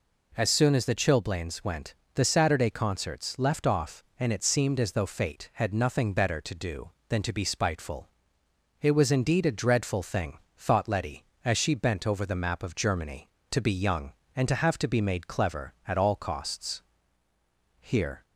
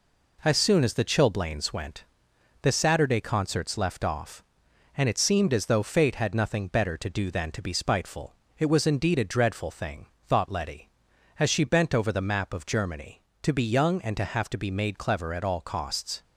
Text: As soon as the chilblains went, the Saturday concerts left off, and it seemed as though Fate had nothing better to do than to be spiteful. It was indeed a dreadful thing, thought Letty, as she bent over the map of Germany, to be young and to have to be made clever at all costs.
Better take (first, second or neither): second